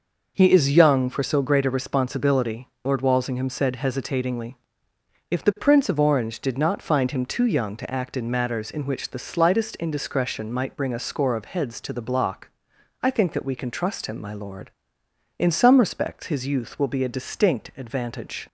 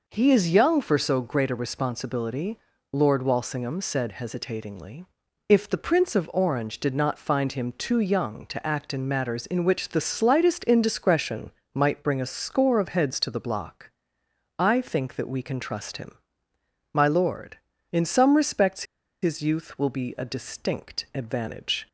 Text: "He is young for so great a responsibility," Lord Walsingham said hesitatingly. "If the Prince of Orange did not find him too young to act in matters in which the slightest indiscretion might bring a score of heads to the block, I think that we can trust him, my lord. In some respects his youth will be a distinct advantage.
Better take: first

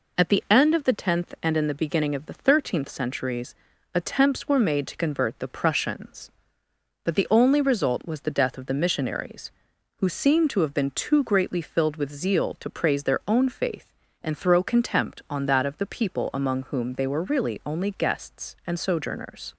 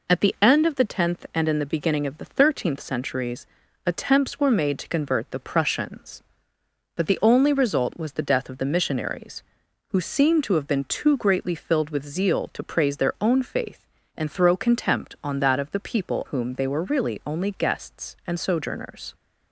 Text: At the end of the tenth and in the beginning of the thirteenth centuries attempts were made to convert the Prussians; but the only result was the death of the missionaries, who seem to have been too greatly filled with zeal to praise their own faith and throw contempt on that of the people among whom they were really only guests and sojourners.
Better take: first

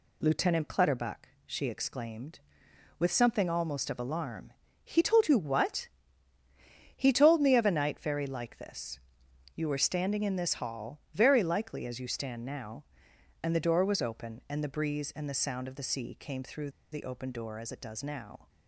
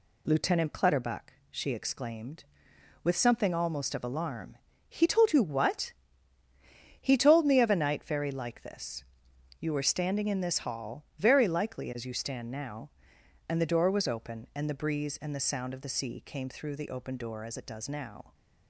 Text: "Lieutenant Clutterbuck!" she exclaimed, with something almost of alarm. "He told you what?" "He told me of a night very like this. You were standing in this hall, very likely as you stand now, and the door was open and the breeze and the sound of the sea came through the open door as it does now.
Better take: second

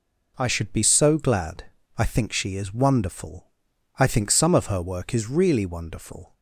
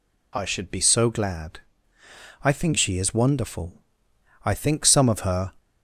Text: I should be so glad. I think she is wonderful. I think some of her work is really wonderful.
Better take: first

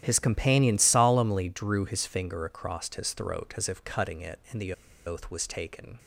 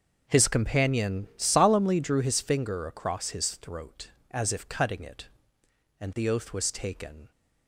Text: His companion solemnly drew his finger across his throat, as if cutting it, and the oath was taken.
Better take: second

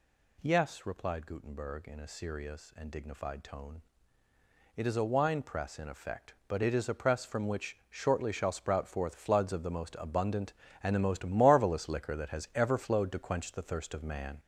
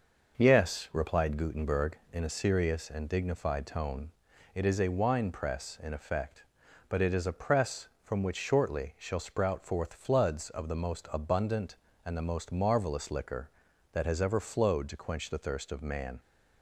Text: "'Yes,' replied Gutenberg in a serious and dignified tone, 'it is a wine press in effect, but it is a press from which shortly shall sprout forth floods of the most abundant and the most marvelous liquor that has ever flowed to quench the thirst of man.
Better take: second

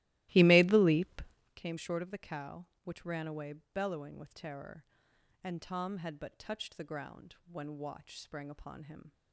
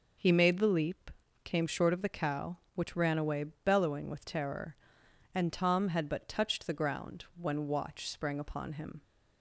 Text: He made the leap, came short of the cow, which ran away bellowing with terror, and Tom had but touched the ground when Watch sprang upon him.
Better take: second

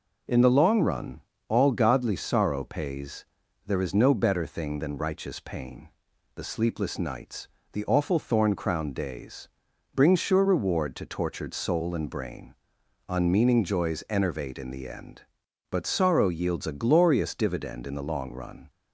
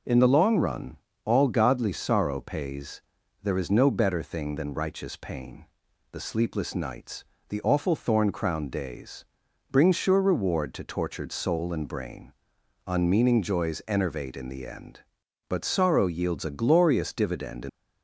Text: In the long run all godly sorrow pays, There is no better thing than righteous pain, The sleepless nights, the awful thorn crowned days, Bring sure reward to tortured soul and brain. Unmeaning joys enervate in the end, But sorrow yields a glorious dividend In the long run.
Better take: first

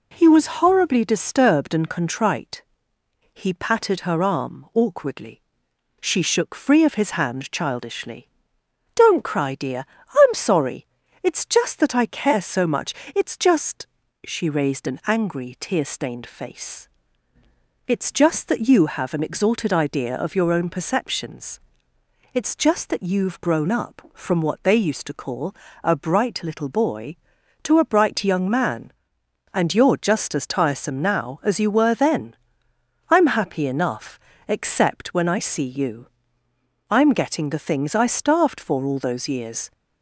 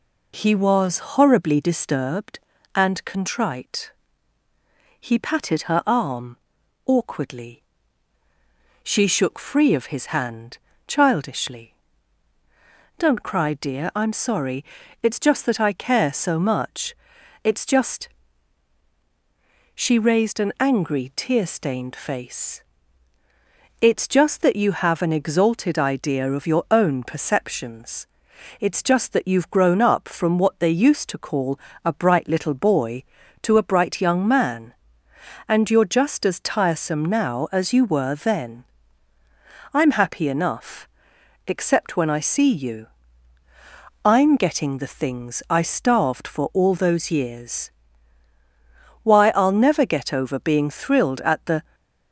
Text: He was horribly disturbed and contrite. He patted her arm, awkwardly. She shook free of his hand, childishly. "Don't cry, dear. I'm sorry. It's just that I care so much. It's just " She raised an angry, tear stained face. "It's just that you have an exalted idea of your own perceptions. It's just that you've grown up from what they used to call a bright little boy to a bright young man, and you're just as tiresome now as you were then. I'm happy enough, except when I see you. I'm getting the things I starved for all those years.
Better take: first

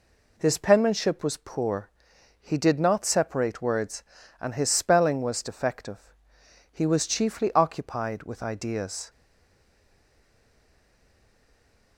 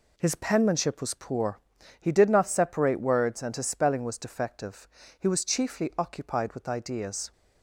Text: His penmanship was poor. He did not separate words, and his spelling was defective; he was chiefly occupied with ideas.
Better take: second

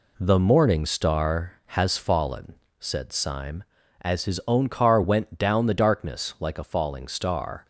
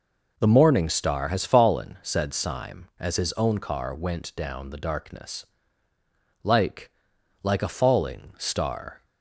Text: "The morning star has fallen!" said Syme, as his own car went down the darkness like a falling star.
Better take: first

